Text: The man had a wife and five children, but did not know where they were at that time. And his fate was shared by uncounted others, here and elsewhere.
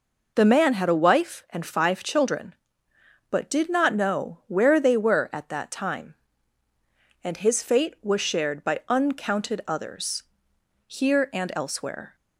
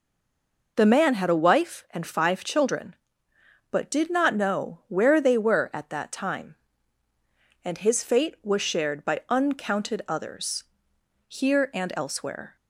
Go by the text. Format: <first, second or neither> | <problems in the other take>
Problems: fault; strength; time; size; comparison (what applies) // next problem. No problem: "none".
first | stays silent before the first word; slight; until 0.7 s; 0.7 s long